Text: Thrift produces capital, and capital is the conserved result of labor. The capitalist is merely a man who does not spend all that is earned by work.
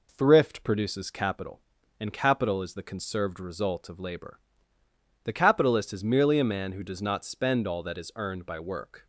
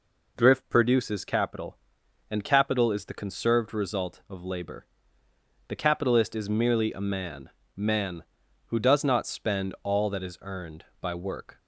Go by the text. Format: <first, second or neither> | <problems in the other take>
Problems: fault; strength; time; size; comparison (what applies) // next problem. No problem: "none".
first | says "man" twice; at 7.7 s